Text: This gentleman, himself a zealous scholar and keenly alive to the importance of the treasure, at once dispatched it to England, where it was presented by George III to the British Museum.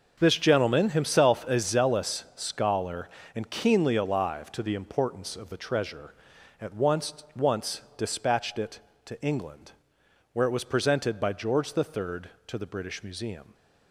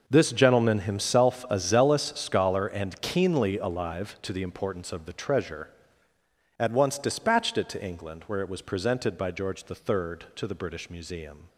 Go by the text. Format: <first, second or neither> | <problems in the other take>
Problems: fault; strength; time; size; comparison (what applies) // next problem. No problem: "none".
second | starts louder than the rest; until 1.2 s; 6 dB // says "once" twice; at 7.3 s